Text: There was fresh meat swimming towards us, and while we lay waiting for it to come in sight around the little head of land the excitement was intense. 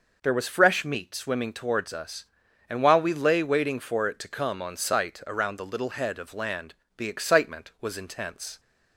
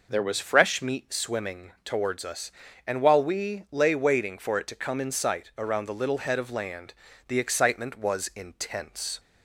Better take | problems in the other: second | says "on" for "in"; at 4.5 s // pauses between "land" and "the"; slight; at 6.7 s; 0.24 s long; slight in the second

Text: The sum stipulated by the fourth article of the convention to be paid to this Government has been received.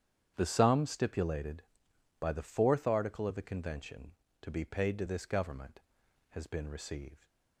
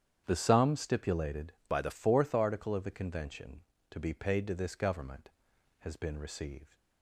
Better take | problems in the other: first | starts louder than the rest; strong; until 1.2 s; 9.5 dB; strong in the first // changes voice from "by" to "the"; from 1.6 to 1.9 s; 0.3 s long

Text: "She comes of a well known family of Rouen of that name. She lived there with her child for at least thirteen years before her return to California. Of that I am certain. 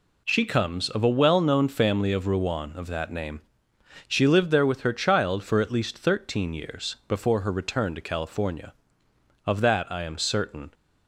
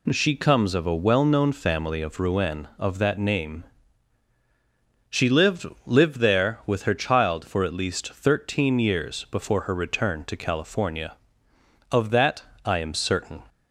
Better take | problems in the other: first | says "lived" twice; at 5.8 s // pauses between "that" and "I"; slight; at 12.4 s; 0.20 s long

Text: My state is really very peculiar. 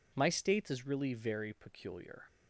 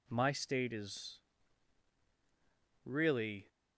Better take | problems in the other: first | pauses between "is" and "really"; strong; at 1.1 s; 1.6 s long // stops before "very peculiar"; at 3.4 s

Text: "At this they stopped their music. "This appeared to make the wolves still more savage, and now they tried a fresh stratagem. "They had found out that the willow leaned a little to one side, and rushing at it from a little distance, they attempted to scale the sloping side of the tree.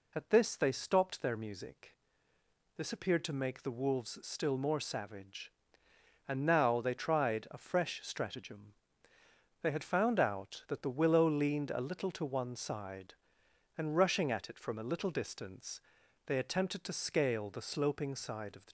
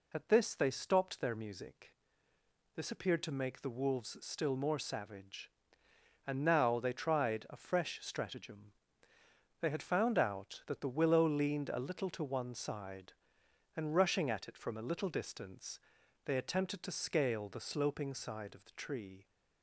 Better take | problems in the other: second | stops before "tree"; at 18.6 s

